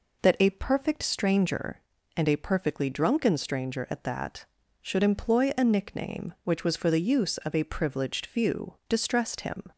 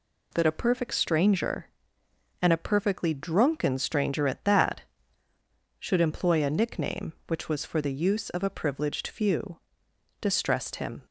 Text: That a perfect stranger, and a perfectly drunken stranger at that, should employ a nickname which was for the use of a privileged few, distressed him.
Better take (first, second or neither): neither